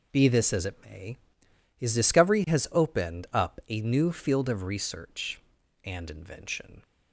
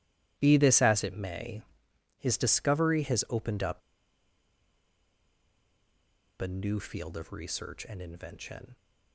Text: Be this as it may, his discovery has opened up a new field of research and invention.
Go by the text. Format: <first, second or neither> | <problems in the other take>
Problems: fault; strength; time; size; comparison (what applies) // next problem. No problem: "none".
first | starts louder than the rest; strong; until 1.3 s; 14 dB // pauses between "up" and "a"; strong; at 3.8 s; 2.5 s long